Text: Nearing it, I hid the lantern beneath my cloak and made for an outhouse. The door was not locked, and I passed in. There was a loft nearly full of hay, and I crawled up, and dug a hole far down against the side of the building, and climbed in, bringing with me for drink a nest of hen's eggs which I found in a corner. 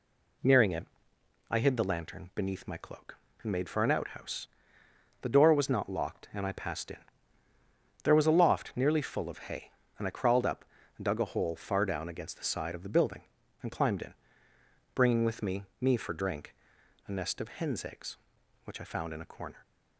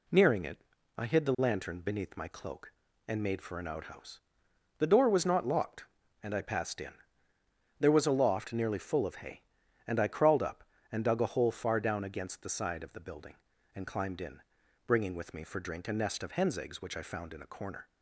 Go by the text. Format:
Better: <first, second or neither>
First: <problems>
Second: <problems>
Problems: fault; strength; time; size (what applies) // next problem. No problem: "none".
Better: second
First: says "me" twice; at 15.7 s // pauses between "drink" and "a"; noticeable; at 16.5 s; 0.52 s long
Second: none